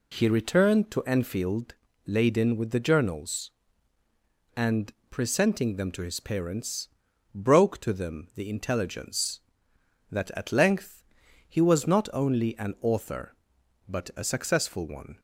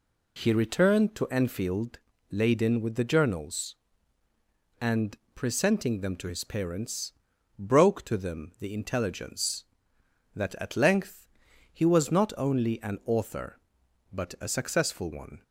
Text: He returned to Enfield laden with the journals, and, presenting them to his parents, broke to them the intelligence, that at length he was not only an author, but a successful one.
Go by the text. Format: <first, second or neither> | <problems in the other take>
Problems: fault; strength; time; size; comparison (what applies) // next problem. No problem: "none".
neither | pauses between "Enfield" and "laden"; slight; the same in both // pauses between "length" and "he"; noticeable; the same in both